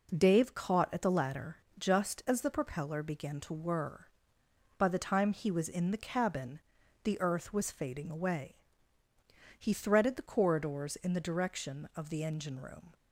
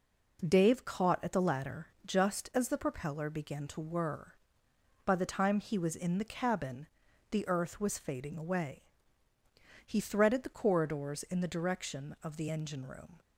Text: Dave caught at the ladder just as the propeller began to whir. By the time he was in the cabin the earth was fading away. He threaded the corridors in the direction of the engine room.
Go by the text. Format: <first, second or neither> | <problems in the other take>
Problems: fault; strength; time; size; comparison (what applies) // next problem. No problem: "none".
neither | pauses between "ladder" and "just"; slight; the same in both // pauses between "cabin" and "the"; the same in both